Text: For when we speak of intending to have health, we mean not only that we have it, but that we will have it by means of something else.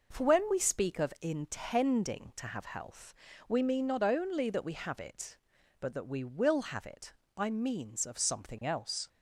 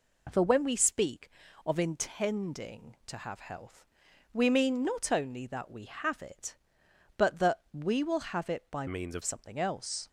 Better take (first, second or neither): first